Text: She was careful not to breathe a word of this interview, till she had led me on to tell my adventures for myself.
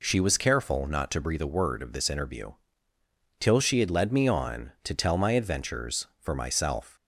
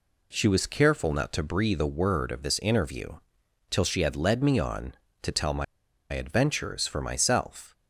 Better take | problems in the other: first | pauses between "my" and "adventures"; noticeable; at 5.6 s; 0.47 s long

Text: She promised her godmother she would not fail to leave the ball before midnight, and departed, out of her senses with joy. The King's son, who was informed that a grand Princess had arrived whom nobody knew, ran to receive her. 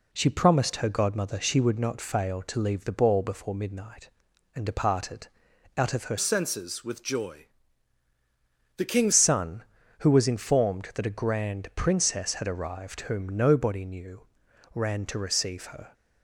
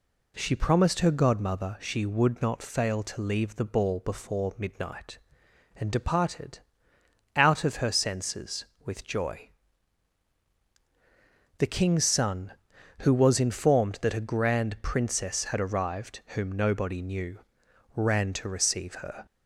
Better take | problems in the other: second | changes voice from "senses" to "King's"; from 6.1 to 9.1 s; 3.0 s long

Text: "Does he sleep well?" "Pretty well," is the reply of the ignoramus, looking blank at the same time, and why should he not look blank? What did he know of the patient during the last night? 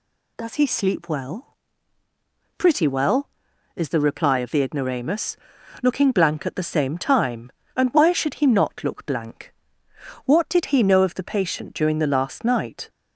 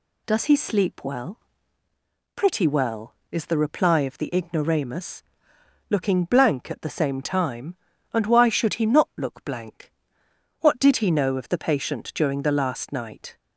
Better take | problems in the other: neither | none

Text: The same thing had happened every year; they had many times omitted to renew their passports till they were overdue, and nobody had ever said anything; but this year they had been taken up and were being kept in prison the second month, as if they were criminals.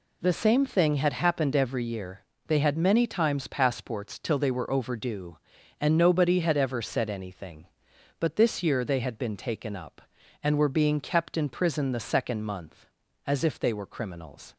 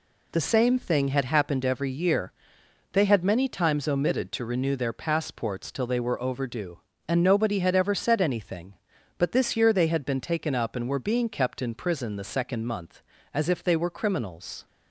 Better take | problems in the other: second | skips "omitted to renew their"; at 3.4 s

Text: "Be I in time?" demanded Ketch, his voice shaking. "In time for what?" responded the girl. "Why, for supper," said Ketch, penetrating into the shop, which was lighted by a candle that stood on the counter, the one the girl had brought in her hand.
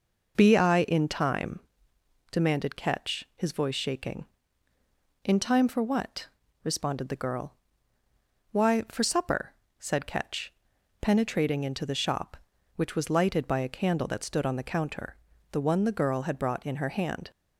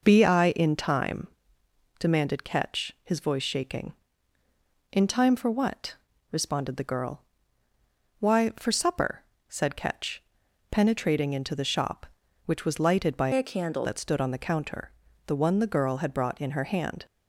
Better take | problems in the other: first | changes voice from "a" to "candle"; from 13.3 to 13.8 s; 0.5 s long

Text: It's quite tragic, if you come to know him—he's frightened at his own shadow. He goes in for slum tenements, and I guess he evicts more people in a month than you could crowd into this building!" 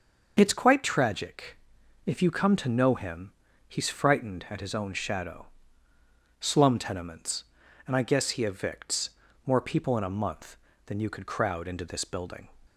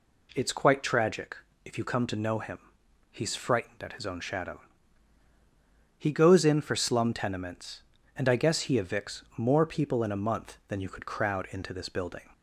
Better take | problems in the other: second | starts louder than the rest; until 1.3 s; 6.5 dB // skips "He goes in for"; at 5.9 s // pauses between "evicts" and "more"; at 9.0 s; 0.38 s long

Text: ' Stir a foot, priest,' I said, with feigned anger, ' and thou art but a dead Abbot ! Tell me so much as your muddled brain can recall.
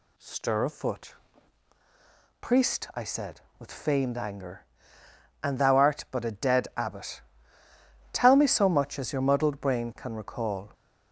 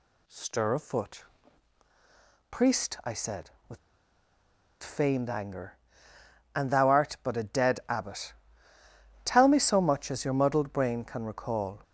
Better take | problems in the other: first | pauses between "with" and "feigned"; at 3.7 s; 1.0 s long

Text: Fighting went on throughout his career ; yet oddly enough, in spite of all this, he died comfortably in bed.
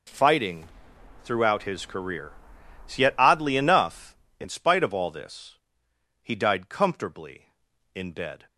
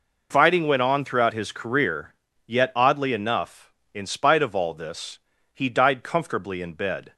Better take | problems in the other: second | skips "went on"; at 0.9 s

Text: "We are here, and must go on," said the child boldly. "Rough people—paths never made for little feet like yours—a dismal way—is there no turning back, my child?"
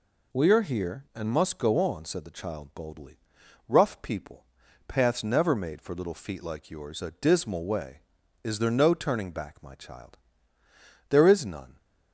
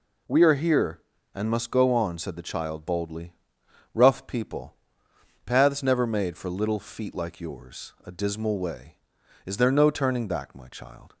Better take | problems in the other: second | goes on to say "There is none"; noticeable; from 11.1 s on; 0.66 s long

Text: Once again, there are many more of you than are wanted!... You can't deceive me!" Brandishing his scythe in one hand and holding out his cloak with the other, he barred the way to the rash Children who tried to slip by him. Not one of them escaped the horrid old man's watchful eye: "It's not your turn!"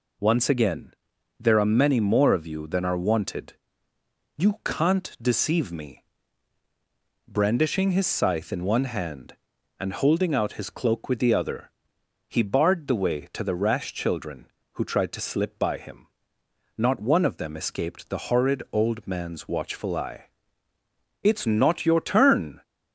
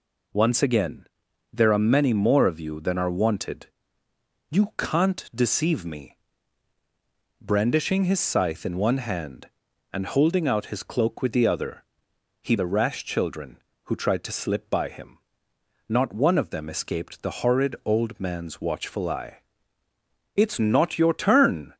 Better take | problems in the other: first | skips "barred the way to"; at 12.5 s

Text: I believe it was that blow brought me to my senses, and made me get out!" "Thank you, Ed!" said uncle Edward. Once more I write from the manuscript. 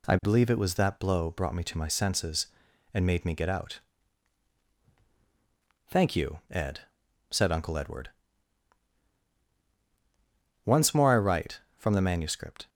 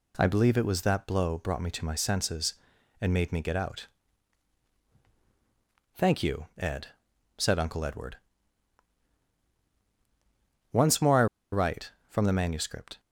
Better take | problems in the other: first | pauses between "I" and "write"; slight; at 11.2 s; 0.26 s long

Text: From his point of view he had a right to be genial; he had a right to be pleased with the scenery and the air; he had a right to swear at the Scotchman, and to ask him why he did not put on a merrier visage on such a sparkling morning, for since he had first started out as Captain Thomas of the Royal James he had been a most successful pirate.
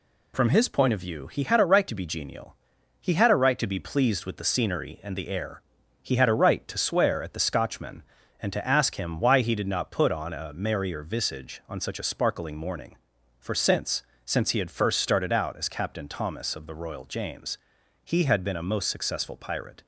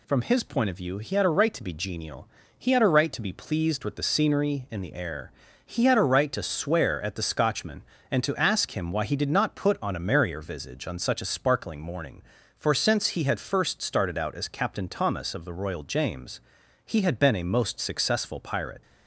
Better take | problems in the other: second | says "since" twice; at 14.2 s // pauses between "James" and "he"; noticeable; at 17.5 s; 0.46 s long; noticeable in the second

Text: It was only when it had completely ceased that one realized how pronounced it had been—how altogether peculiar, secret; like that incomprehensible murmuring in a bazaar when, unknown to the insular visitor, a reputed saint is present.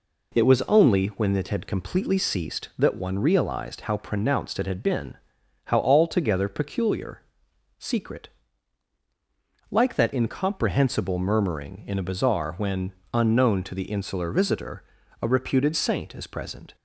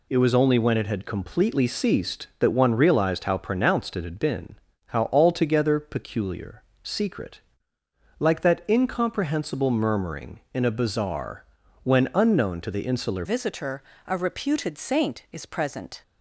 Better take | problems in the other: first | pauses between "bazaar" and "when"; at 11.4 s; 0.40 s long // changes voice at "visitor"; from 13.2 s on; 2.8 s long

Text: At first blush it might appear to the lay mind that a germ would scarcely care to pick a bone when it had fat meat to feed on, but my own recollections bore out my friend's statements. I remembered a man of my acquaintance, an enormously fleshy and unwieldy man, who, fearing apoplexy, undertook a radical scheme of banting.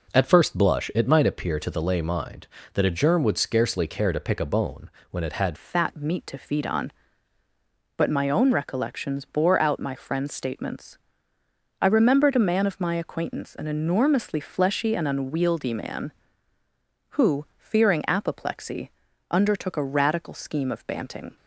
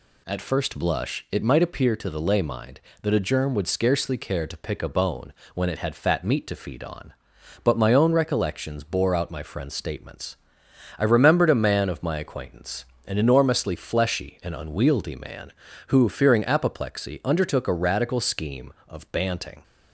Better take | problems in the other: second | pauses between "bone" and "when"; slight; at 4.8 s; 0.22 s long; slight in the second // changes voice at "fat"; from 5.5 s on; 15.8 s long

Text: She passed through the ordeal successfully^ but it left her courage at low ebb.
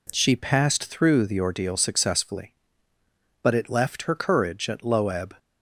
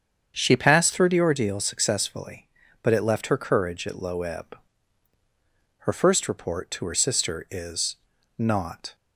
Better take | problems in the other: first | starts louder than the rest; strong; until 1.3 s; 7.5 dB // goes on to say "Her first report to her sister is not"; strong; from 5.8 s on; 3.0 s long

